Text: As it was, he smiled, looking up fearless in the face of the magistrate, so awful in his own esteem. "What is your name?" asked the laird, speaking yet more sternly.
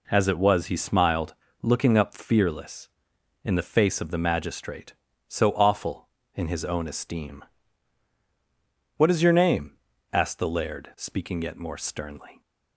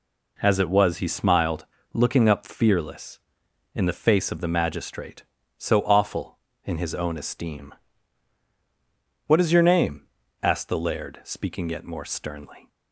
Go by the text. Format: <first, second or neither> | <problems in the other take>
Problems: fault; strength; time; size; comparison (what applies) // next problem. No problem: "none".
neither | none